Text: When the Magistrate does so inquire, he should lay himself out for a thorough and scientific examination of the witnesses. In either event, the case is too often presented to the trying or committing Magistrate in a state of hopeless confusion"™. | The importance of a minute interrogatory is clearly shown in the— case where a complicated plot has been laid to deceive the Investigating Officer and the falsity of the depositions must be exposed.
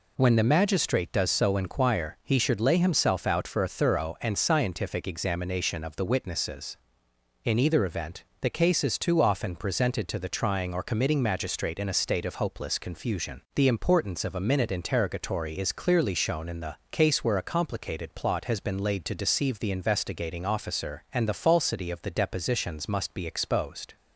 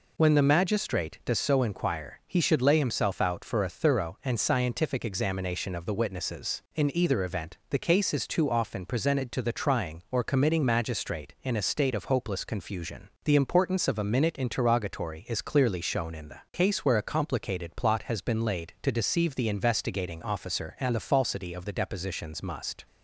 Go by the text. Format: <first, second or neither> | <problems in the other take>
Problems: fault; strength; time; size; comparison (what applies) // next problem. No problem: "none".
first | stops before "be exposed"; at 22.8 s